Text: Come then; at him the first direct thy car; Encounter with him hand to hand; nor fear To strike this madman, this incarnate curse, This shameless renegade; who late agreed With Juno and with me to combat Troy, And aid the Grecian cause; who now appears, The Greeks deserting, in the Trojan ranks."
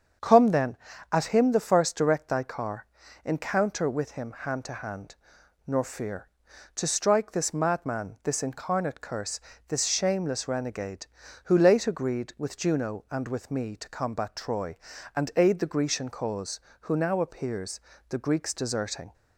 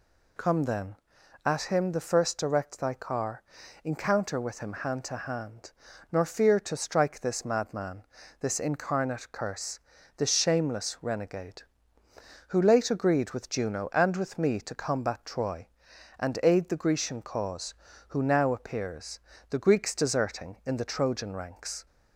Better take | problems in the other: second | starts louder than the rest; strong; until 1.5 s; 7.5 dB // stops before "in the Trojan ranks"; at 19.1 s

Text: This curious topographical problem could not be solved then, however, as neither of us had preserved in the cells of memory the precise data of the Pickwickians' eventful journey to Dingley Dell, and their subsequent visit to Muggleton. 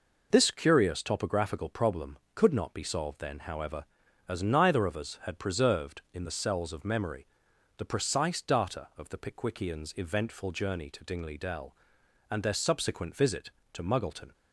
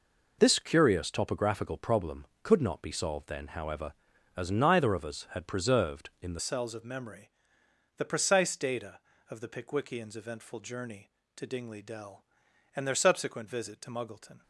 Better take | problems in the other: first | changes voice at "cells"; from 6.3 s on; 8.1 s long // pauses between "memory" and "the"; noticeable; at 7.3 s; 0.66 s long; noticeable in the first

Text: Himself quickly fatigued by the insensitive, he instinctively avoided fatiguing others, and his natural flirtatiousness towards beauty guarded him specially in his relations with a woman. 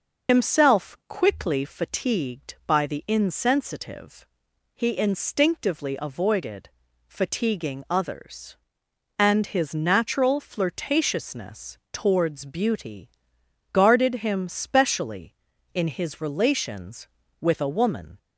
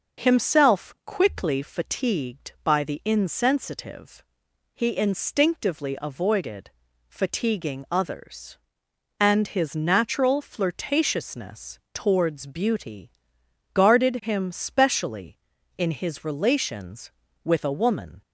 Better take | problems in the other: second | loses the start of "Himself"; at 0.2 s; 90 ms // pauses between "avoided" and "fatiguing"; slight; at 6.6 s; 0.36 s long; slight in the second // pauses between "flirtatiousness" and "towards"; slight; at 11.7 s; 0.16 s long; slight in the second // pauses between "beauty" and "guarded"; noticeable; at 13.0 s; 0.62 s long; noticeable in the second

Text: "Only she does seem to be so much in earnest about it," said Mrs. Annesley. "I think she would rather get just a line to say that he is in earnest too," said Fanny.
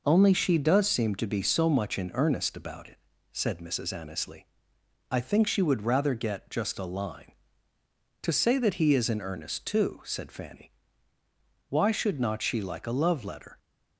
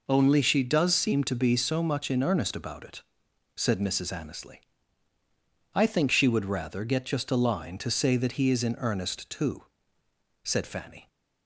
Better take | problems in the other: second | goes on to say "Why should not she like a love letter"; strong; from 11.6 s on; 1.8 s long

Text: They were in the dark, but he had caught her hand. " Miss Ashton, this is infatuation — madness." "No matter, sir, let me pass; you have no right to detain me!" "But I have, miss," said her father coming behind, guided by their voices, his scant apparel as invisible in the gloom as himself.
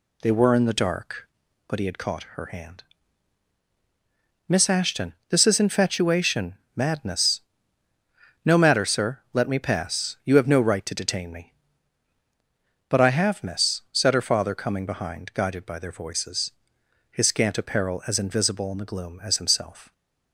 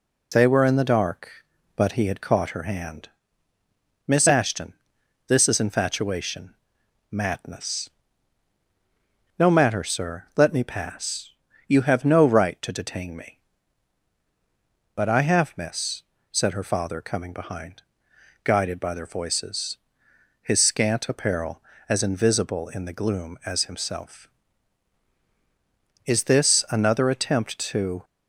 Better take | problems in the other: first | goes on to say "Is this another attempt to"; strong; from 26.0 s on; 1.9 s long

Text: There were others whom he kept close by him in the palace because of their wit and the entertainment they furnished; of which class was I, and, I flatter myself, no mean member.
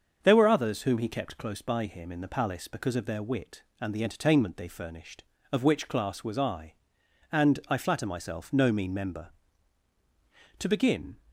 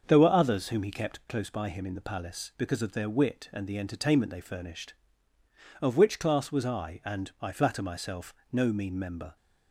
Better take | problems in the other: second | starts louder than the rest; until 1.2 s; 7 dB; also in the second // goes on to say "To begin"; from 10.5 s on; 0.60 s long

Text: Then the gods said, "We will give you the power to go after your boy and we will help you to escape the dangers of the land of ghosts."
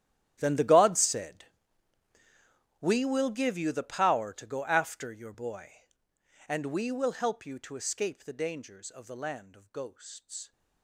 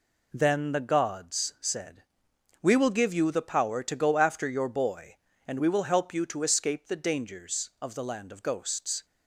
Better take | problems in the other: second | gets quieter; strong; throughout; 19.5 dB

